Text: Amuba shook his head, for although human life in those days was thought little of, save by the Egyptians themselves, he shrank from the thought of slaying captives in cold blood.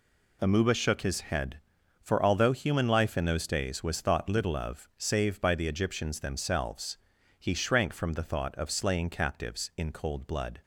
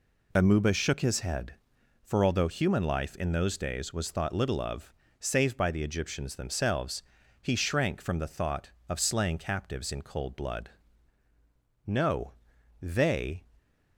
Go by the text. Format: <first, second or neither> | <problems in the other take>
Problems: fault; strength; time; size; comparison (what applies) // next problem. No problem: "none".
first | goes on to say "No they"; from 11.8 s on; 1.5 s long